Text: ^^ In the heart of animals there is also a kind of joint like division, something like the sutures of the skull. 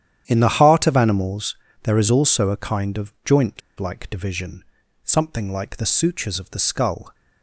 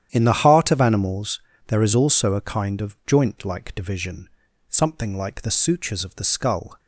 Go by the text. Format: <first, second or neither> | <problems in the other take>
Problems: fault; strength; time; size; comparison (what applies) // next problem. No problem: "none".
second | starts louder than the rest; strong; until 1.2 s; 10 dB; strong in the second // pauses between "animals" and "there"; slight; at 1.5 s; 0.28 s long; slight in the second // pauses between "joint" and "like"; slight; at 3.6 s; 0.19 s long